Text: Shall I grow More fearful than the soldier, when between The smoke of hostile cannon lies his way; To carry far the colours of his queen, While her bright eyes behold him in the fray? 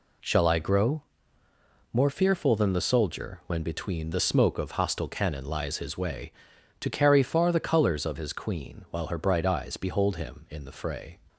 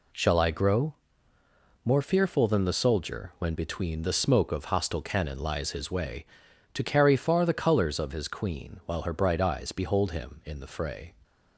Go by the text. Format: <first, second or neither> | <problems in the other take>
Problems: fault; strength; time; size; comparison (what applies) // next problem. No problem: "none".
neither | pauses between "grow" and "More"; noticeable; the same in both